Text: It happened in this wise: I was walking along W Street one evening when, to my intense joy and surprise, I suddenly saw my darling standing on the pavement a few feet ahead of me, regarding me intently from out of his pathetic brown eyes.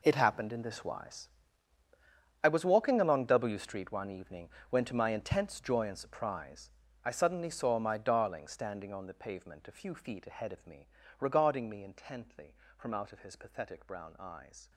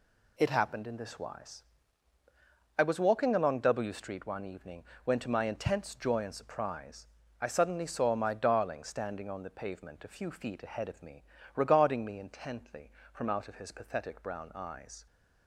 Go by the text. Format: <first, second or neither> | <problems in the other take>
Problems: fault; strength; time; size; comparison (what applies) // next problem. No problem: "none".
second | gets quieter; strong; throughout; 15.5 dB // pauses between "evening" and "when"; slight; at 4.4 s; 0.22 s long; slight in the second